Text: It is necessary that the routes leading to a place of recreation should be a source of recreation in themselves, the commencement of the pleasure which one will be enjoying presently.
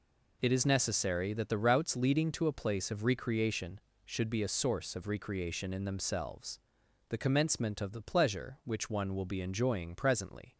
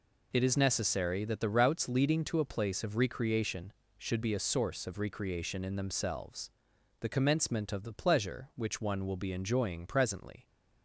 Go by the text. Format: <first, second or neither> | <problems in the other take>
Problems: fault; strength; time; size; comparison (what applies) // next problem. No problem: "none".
neither | none